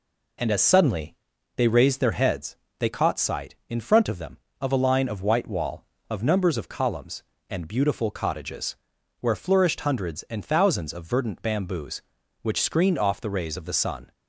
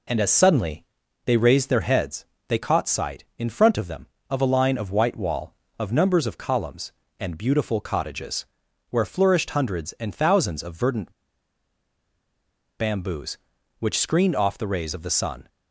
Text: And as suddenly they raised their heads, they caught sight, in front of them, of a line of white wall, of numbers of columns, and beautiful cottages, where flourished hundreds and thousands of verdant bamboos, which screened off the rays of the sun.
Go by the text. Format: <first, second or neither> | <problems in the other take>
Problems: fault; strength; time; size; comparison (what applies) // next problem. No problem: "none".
first | pauses between "suddenly" and "they"; at 0.8 s; 0.42 s long; also in the first // pauses between "verdant" and "bamboos"; strong; at 11.1 s; 1.6 s long